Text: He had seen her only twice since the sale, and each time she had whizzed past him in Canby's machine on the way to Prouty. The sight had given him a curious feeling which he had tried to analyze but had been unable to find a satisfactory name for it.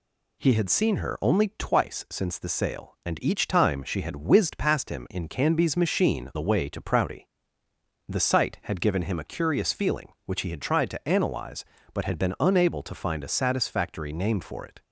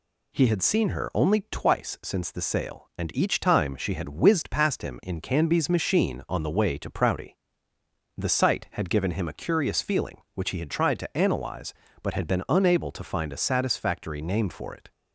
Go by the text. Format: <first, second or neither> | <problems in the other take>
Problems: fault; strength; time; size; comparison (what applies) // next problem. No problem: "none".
second | skips "on"; at 6.3 s